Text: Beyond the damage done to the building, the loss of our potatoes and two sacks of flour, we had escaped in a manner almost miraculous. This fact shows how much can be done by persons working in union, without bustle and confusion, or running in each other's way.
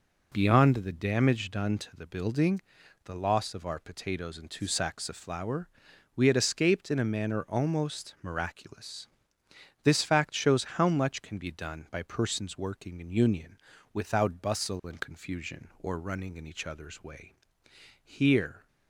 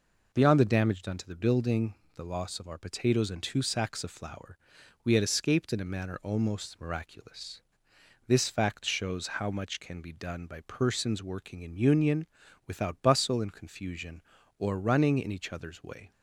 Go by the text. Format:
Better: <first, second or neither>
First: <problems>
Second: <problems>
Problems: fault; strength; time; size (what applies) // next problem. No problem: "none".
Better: second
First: goes on to say "Here"; noticeable; from 18.0 s on; 0.64 s long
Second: none